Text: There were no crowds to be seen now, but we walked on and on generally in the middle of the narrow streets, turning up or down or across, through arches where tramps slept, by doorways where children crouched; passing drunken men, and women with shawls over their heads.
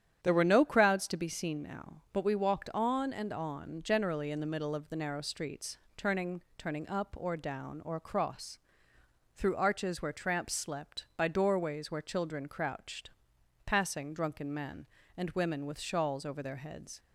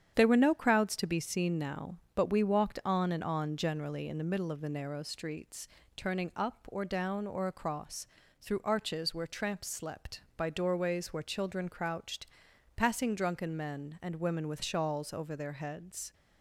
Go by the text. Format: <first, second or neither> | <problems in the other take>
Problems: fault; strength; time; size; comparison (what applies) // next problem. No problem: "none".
second | starts louder than the rest; strong; until 1.2 s; 9.5 dB; strong in the second // says "turning" twice; at 6.5 s